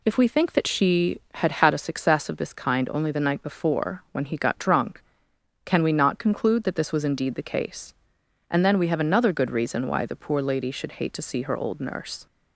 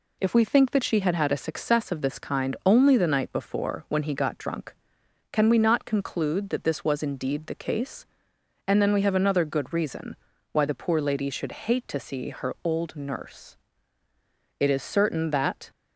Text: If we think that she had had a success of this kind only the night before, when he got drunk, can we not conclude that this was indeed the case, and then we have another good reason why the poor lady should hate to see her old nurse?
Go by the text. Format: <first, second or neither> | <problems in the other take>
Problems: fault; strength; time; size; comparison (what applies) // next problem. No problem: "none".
first | pauses between "reason" and "why"; slight; at 10.1 s; 0.34 s long // goes on to say "It is certain that"; noticeable; from 14.6 s on; 1.1 s long